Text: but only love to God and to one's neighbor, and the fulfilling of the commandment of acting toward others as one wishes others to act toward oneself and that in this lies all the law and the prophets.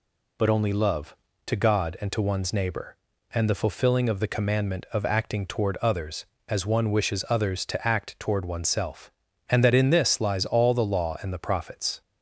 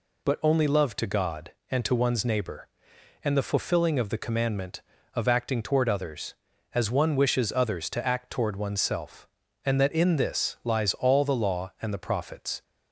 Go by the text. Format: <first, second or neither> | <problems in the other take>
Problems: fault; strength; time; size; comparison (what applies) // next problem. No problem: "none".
neither | none